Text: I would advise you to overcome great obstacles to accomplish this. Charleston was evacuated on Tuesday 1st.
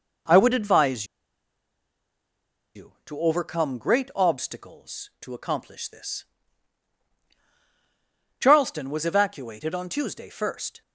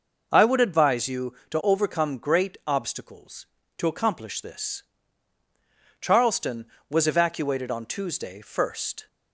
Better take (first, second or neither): second